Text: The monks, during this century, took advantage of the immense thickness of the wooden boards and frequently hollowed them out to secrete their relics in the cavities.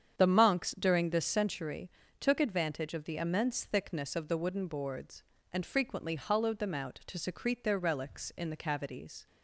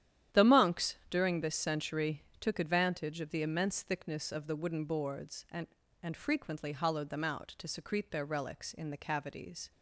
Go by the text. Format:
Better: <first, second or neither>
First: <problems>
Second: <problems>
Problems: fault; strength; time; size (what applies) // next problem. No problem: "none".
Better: first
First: starts louder than the rest; strong; until 1.2 s; 8 dB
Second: starts louder than the rest; strong; until 1.4 s; 11 dB // says "and" twice; at 6.0 s